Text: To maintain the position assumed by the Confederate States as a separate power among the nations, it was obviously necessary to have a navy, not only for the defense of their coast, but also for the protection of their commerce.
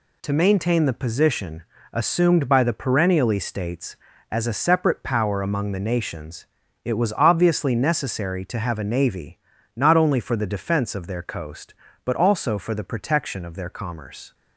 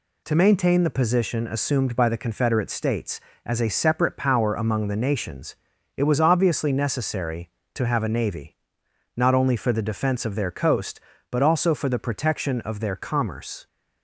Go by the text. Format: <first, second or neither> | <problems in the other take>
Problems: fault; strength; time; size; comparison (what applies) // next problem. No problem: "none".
second | pauses between "position" and "assumed"; slight; at 1.6 s; 0.30 s long // says "Perennially" for "Confederate"; at 2.7 s